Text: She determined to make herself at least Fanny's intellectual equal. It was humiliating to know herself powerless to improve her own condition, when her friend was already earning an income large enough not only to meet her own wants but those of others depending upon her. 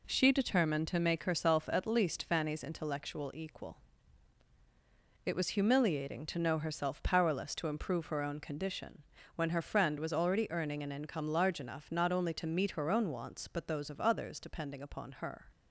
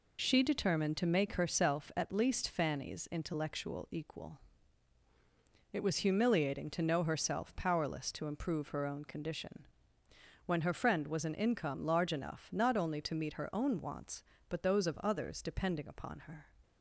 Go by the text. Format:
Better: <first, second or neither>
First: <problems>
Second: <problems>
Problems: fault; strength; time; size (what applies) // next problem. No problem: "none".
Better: first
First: none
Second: skips "already earning"; at 11.2 s